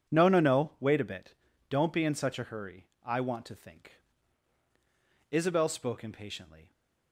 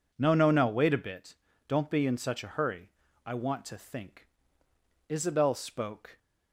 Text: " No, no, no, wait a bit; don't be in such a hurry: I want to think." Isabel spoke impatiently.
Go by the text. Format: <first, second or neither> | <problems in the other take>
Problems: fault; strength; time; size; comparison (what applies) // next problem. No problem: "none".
first | stops before "impatiently"; at 6.1 s